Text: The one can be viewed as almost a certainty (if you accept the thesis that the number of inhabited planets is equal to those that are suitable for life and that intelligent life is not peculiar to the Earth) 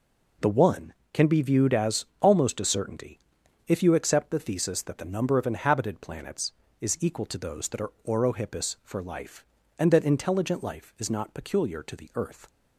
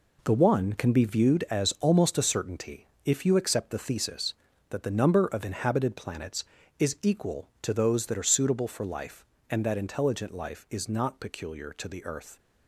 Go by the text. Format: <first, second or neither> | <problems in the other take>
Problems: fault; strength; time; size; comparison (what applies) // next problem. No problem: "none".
second | pauses between "as" and "almost"; slight; at 2.0 s; 0.16 s long // says "orohippus" for "suitable"; at 8.0 s